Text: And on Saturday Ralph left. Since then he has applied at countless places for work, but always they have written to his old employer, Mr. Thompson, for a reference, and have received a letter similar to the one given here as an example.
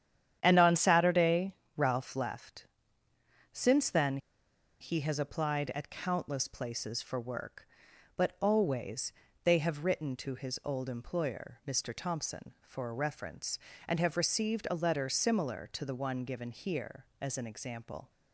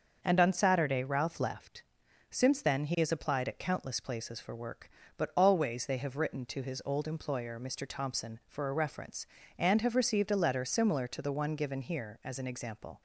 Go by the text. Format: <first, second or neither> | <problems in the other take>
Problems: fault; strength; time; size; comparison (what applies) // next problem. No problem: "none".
second | starts louder than the rest; strong; until 1.4 s; 9.5 dB; also in the second // pauses between "Saturday" and "Ralph"; slight; at 1.5 s; 0.22 s long // pauses between "then" and "he"; noticeable; at 4.1 s; 0.63 s long // pauses between "always" and "they"; slight; at 9.1 s; 0.34 s long